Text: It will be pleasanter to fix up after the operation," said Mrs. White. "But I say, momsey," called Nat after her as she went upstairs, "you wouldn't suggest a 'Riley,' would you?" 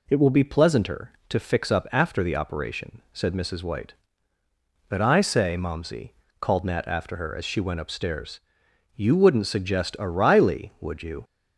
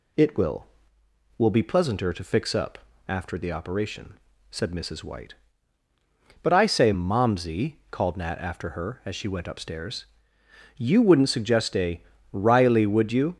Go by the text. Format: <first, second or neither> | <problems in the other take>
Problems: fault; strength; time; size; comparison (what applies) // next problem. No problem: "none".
first | says "will" twice; at 1.3 s // pauses between "up" and "after"; slight; at 2.7 s; 0.30 s long // pauses between "a" and "Riley"; slight; at 12.0 s; 0.30 s long